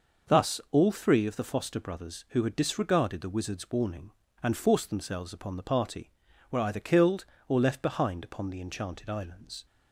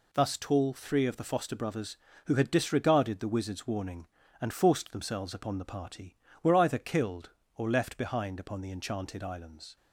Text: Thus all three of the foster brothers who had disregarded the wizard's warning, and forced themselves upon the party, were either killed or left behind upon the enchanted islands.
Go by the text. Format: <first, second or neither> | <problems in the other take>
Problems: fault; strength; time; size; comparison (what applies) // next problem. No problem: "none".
first | says "tall" for "all"; at 0.3 s